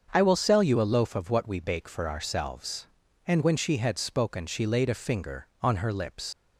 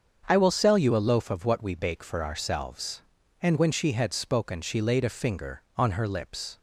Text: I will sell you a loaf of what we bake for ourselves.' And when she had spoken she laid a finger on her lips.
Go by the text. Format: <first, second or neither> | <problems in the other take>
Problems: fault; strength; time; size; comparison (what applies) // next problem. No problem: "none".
second | starts louder than the rest; until 1.1 s; 7 dB; also in the second // leaves "lips" unfinished; at 6.3 s; 105 ms